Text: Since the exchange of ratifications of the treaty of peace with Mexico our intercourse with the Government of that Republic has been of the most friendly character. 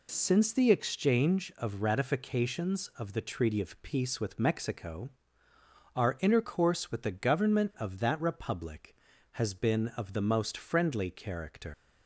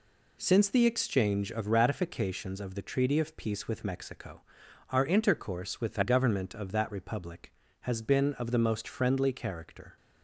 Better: second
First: pauses between "Mexico" and "our"; noticeable; at 5.0 s; 0.84 s long // leaves "character" unfinished; at 11.7 s; 120 ms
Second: pauses between "Mexico" and "our"; noticeable; at 4.4 s; 0.50 s long

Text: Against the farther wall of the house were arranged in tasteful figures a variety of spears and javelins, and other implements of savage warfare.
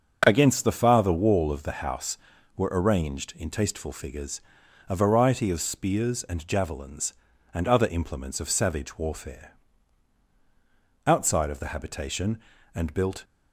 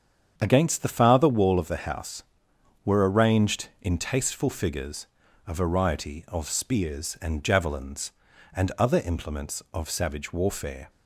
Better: second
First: starts louder than the rest; strong; until 1.2 s; 7 dB // pauses between "figures" and "a"; noticeable; at 4.3 s; 0.48 s long // goes on to say "Outside of the habitation and built"; strong; from 11.0 s on; 2.1 s long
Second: starts louder than the rest; strong; until 1.3 s; 7.5 dB // pauses between "figures" and "a"; at 5.0 s; 0.42 s long

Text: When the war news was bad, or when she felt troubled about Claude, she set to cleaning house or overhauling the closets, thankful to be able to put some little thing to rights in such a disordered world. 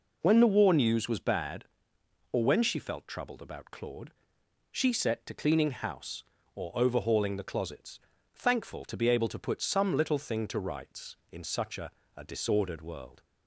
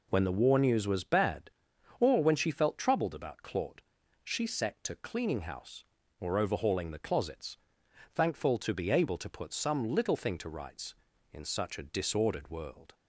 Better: second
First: says "a" twice; at 12.1 s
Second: none

